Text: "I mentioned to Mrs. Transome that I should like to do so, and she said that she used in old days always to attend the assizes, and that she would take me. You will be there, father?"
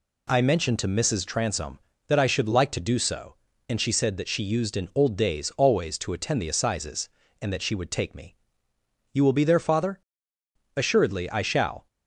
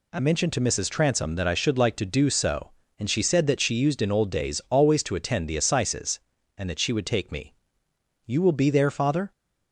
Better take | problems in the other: second | goes on to say "Assuredly I shall"; noticeable; from 10.7 s on; 1.1 s long

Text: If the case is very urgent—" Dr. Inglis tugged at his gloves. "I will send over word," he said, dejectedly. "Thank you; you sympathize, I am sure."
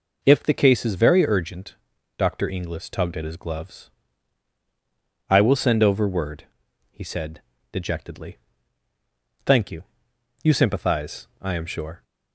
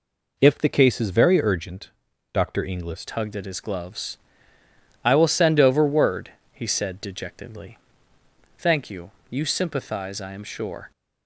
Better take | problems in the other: first | changes voice at "tugged"; from 3.0 s on; 7.9 s long

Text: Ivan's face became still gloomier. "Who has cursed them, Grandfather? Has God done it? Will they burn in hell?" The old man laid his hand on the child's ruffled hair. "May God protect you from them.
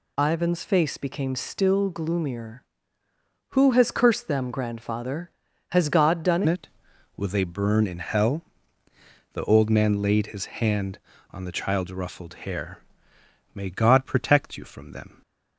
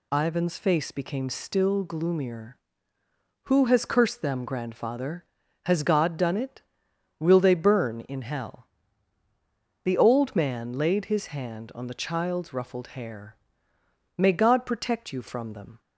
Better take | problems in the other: second | changes voice at "it"; from 6.4 s on; 8.8 s long

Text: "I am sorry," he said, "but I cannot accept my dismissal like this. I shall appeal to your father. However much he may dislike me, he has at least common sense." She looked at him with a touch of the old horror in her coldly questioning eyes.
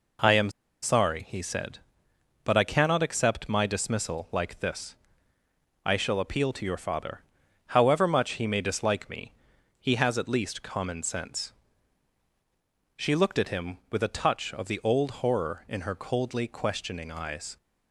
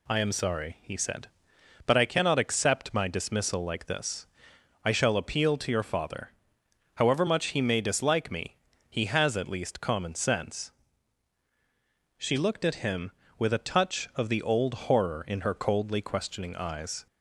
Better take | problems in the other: second | pauses between "am" and "sorry"; slight; at 0.5 s; 0.32 s long

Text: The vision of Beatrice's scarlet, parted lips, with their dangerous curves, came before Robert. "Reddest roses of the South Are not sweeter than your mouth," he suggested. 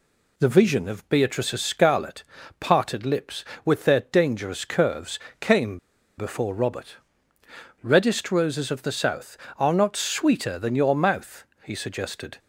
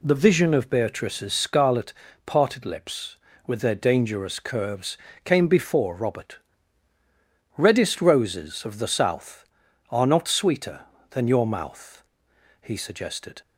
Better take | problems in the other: second | pauses between "came" and "before"; at 5.7 s; 0.40 s long

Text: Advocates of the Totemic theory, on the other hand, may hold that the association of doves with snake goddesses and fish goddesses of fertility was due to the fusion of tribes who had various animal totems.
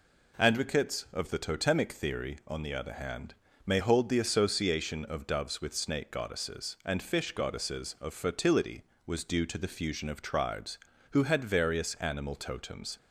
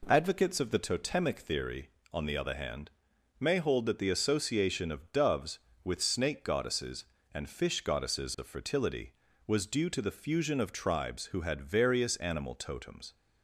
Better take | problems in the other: second | skips "that"; at 4.0 s

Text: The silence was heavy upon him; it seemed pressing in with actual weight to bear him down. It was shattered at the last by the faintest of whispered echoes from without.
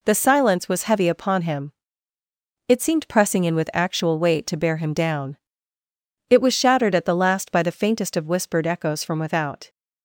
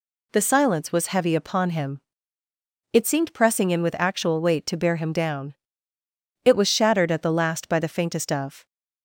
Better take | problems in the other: first | stops before "whispered echoes from without"; at 8.6 s

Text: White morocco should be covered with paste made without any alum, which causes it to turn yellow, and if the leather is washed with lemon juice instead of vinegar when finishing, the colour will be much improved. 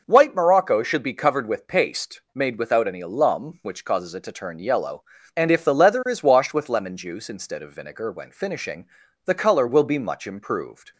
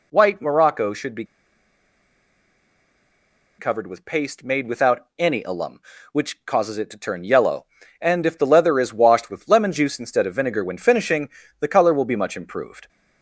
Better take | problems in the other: first | pauses between "be" and "covered"; strong; at 1.2 s; 2.3 s long

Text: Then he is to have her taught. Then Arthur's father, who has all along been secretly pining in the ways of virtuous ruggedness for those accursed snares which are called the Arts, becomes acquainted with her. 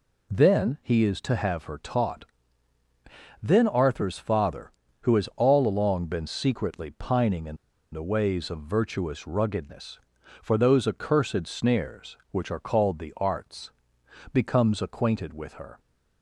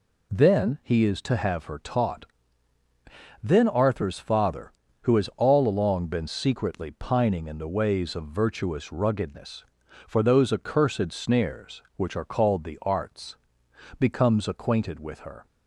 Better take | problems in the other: second | pauses between "in" and "the"; slight; at 7.5 s; 0.35 s long

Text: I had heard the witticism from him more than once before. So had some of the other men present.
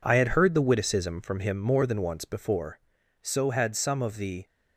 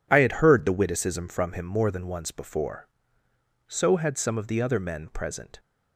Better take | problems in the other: second | stops before "other men present"; at 4.4 s

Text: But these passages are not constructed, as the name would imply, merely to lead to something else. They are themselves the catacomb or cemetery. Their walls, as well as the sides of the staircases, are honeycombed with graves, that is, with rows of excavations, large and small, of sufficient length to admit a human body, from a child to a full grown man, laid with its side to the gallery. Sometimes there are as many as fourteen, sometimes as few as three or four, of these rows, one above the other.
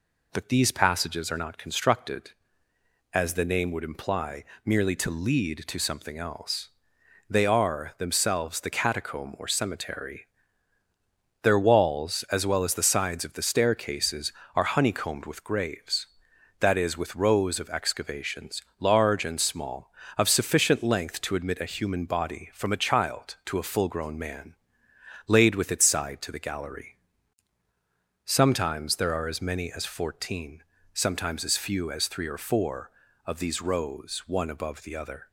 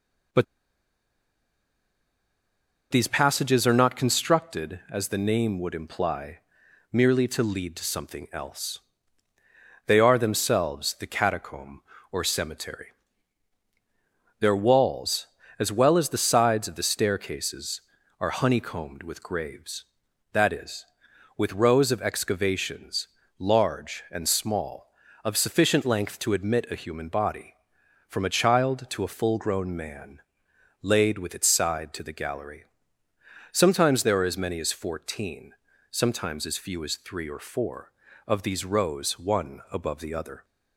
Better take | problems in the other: first | pauses between "But" and "these"; strong; at 0.4 s; 2.4 s long

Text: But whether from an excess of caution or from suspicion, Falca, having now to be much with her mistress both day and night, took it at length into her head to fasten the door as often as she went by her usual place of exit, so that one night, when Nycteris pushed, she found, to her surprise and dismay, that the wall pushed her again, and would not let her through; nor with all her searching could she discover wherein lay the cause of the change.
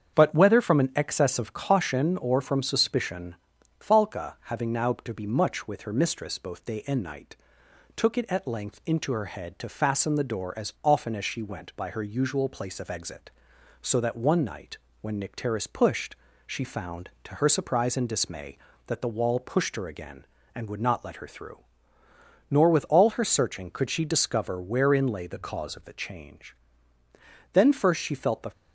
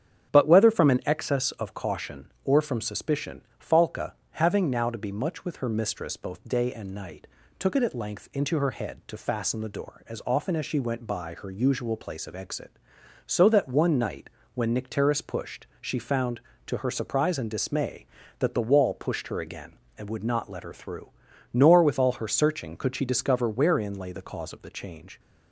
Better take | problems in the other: second | starts louder than the rest; strong; until 1.2 s; 7.5 dB; strong in the second // goes on to say "Then first she felt the"; noticeable; from 27.5 s on; 0.98 s long

